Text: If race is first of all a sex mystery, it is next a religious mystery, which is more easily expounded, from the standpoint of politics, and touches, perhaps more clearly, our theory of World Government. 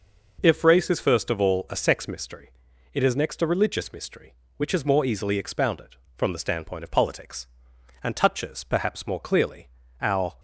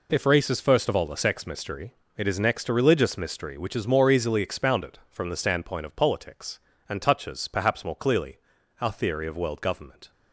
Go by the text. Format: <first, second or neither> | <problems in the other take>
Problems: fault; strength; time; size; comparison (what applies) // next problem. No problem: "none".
second | stops before "theory of World Government"; at 10.3 s